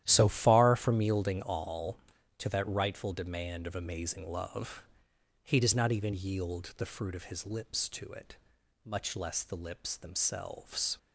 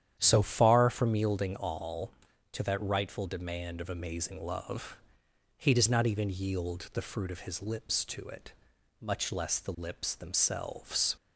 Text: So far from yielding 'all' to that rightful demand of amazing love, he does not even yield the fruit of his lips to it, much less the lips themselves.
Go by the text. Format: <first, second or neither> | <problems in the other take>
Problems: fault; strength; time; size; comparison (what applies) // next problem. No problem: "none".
second | gets quieter; strong; throughout; 12.5 dB // starts louder than the rest; strong; until 1.0 s; 12 dB; strong in the second